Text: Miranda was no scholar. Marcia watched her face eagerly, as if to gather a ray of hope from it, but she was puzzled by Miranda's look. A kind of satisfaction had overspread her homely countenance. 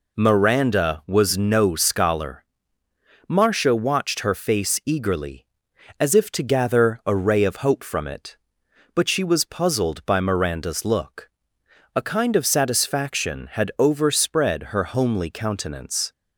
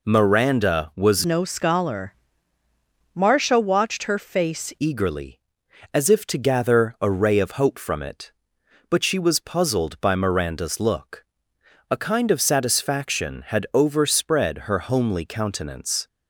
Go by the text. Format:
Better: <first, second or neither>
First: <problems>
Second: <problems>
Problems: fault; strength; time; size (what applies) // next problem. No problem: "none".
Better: first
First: none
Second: changes voice from "no" to "face"; from 1.2 to 4.7 s; 3.5 s long